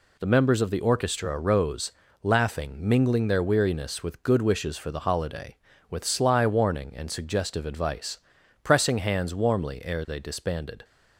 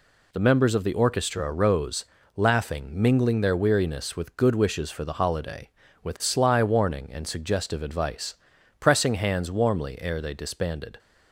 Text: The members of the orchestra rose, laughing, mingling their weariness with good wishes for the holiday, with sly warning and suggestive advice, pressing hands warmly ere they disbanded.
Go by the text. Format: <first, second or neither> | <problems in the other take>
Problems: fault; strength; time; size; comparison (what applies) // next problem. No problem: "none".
neither | none